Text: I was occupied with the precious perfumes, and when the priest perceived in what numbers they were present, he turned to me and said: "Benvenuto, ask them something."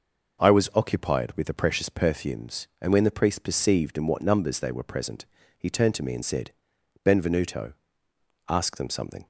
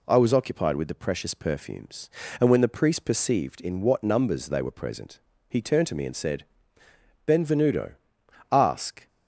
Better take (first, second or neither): first